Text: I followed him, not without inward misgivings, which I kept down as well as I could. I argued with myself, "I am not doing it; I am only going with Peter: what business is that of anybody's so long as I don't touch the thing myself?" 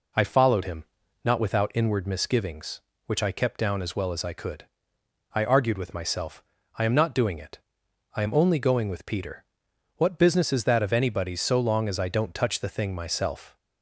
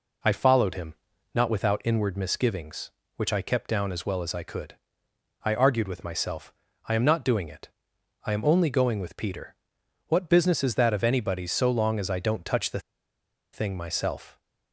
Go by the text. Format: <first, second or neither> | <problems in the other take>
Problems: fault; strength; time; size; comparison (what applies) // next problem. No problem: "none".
first | pauses between "the" and "thing"; noticeable; at 12.7 s; 0.73 s long